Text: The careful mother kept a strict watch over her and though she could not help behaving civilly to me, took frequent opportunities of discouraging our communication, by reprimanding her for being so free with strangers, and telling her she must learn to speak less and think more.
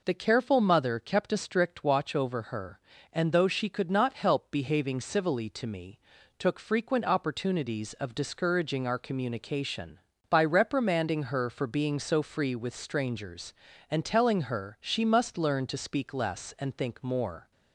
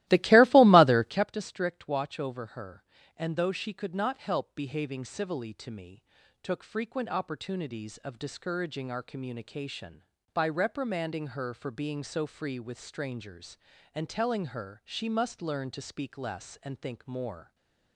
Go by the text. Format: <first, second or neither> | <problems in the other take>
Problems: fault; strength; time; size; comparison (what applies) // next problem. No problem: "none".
first | starts louder than the rest; strong; until 1.3 s; 16.5 dB // stays silent after the last word; slight; from 17.4 s on; 0.5 s long